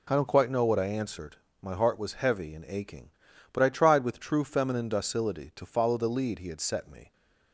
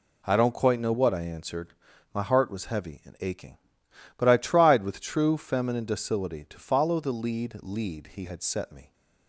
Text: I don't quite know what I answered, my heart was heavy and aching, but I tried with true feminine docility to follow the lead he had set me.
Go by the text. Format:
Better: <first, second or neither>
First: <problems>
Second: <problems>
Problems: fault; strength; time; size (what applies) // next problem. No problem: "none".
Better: first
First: none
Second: says "lead" twice; at 7.6 s